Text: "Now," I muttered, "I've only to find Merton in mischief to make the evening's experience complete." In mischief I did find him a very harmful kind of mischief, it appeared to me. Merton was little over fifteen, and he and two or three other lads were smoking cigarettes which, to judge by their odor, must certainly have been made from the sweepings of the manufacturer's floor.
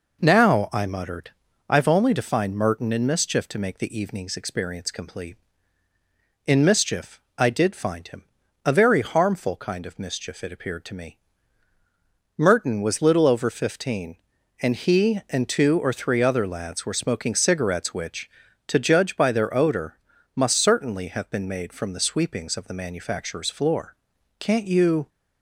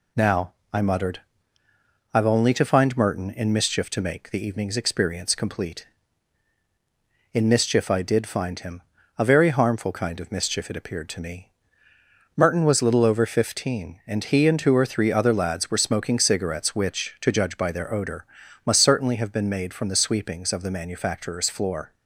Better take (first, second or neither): second